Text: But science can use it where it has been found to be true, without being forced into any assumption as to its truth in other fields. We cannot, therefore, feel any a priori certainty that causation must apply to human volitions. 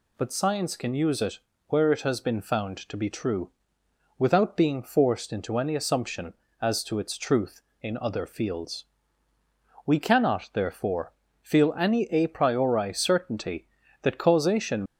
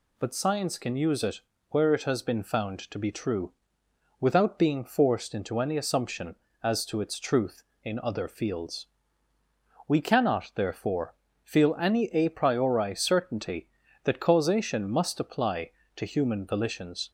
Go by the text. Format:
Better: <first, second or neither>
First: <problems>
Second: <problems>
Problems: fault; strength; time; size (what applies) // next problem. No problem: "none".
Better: second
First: pauses between "it" and "where"; slight; at 1.3 s; 0.30 s long // stops before "must apply to human volitions"; at 14.8 s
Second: pauses between "it" and "where"; slight; at 1.4 s; 0.30 s long